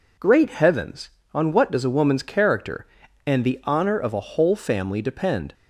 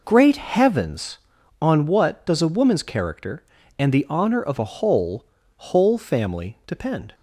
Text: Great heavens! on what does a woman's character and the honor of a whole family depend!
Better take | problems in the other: first | says "whole" twice; at 5.5 s

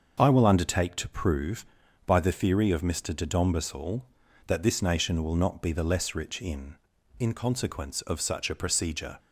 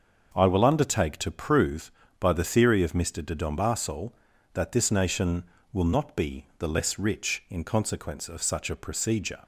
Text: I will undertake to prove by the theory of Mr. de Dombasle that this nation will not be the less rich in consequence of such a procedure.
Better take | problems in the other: second | starts louder than the rest; until 1.1 s; 6.5 dB; also in the second // says "in" twice; at 7.2 s

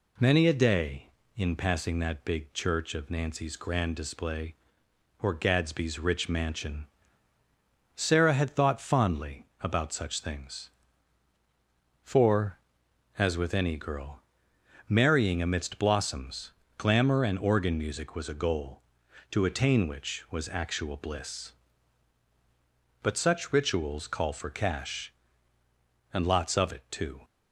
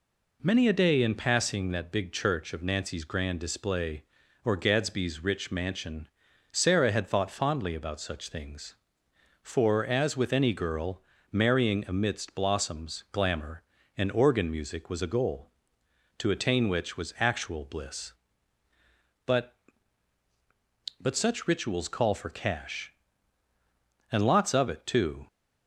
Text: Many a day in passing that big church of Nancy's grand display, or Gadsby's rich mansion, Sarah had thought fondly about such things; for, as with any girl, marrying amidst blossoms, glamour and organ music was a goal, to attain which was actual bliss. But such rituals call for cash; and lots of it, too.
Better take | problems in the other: first | says "But" twice; at 21.0 s

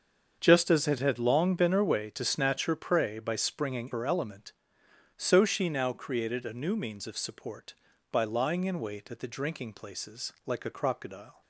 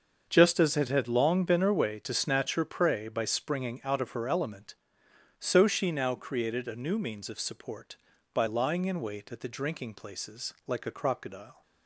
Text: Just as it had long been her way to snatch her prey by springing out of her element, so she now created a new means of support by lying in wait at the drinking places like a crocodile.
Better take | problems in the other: second | starts louder than the rest; until 1.4 s; 7 dB; also in the second // skips "out of"; at 3.9 s

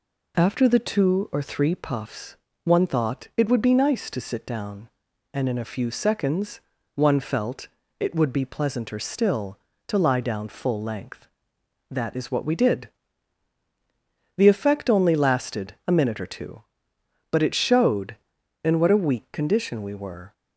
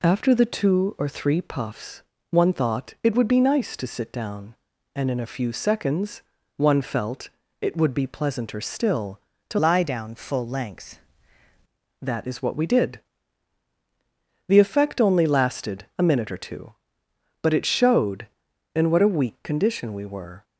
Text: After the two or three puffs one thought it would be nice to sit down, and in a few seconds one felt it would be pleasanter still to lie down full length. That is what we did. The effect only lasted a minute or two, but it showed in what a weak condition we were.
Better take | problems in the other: first | pauses between "puffs" and "one"; slight; at 2.0 s; 0.30 s long; slight in the first // pauses between "seconds" and "one"; slight; at 6.2 s; 0.34 s long; slight in the first // pauses between "felt" and "it"; slight; at 7.2 s; 0.32 s long; slight in the first // changes voice from "lie" to "length"; from 9.5 to 10.9 s; 1.4 s long

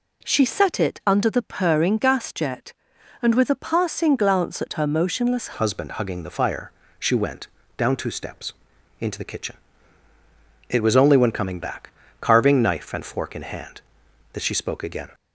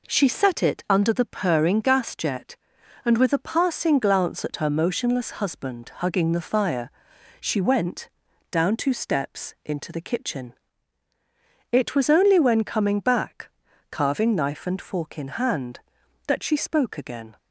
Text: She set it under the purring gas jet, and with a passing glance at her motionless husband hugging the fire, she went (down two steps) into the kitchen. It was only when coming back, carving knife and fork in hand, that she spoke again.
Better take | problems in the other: second | changes voice at "husband"; from 5.5 s on; 9.5 s long

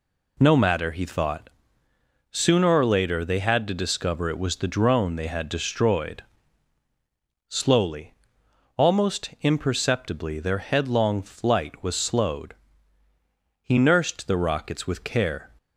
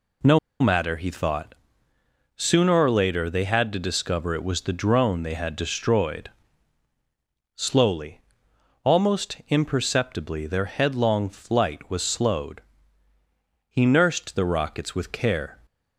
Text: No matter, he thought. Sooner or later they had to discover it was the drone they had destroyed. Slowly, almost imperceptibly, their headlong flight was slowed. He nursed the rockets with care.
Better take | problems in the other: first | pauses between "No" and "matter"; slight; at 0.3 s; 0.22 s long

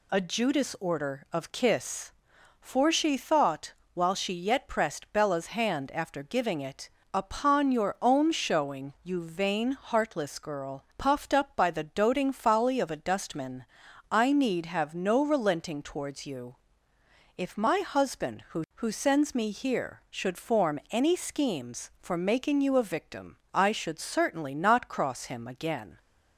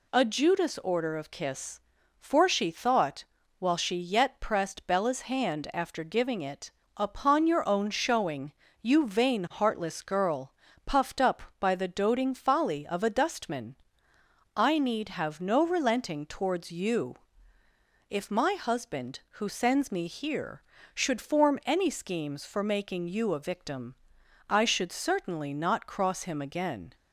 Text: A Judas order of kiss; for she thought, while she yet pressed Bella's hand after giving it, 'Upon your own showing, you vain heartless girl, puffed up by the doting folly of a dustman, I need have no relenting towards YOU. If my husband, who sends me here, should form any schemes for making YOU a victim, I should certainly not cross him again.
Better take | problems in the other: second | says "who" twice; at 18.7 s

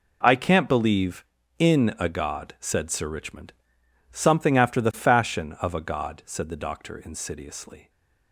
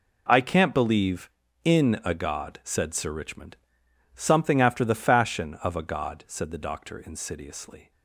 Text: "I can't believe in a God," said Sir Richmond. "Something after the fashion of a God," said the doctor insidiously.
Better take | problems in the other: neither | none

